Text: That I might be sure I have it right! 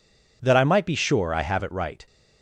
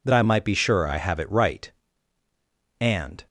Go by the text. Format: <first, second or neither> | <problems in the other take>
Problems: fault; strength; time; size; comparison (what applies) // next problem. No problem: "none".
first | goes on to say "And"; slight; from 2.7 s on; 0.48 s long